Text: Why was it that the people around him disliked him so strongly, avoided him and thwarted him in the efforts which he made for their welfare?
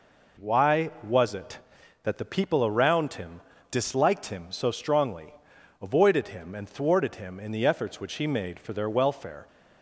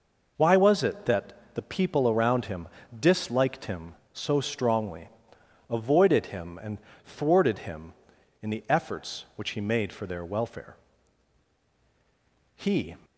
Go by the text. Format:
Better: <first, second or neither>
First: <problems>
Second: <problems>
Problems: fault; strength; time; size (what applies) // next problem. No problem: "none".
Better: first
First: pauses between "him" and "disliked"; slight; at 3.4 s; 0.30 s long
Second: pauses between "that" and "the"; slight; at 1.3 s; 0.20 s long // pauses between "him" and "disliked"; slight; at 2.6 s; 0.30 s long // pauses between "and" and "thwarted"; slight; at 6.7 s; 0.28 s long // goes on to say "He"; slight; from 12.5 s on; 0.40 s long